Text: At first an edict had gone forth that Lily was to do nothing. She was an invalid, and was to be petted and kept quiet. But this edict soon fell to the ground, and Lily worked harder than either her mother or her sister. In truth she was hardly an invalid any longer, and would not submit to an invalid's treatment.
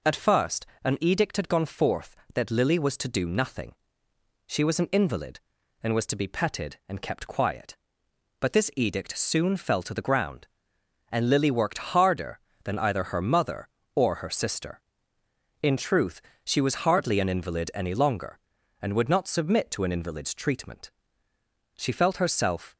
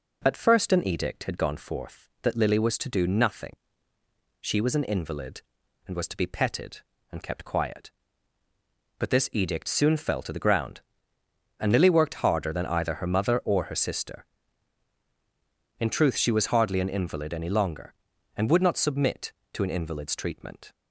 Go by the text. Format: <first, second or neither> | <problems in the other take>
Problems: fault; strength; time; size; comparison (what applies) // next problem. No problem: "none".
second | pauses between "first" and "an"; slight; at 0.6 s; 0.18 s long // pauses between "truth" and "she"; slight; at 16.2 s; 0.24 s long // goes on to say "She felt herself"; noticeable; from 21.7 s on; 0.98 s long